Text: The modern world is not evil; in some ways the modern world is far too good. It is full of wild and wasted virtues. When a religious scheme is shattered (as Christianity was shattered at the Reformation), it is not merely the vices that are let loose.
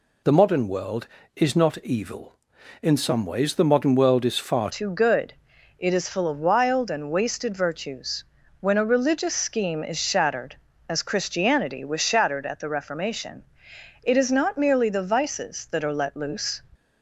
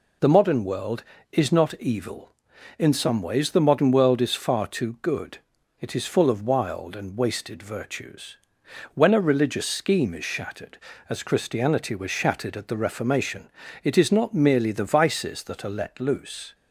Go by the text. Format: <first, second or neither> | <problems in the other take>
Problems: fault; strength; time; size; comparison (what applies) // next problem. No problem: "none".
second | changes voice at "too"; from 4.7 s on; 11.8 s long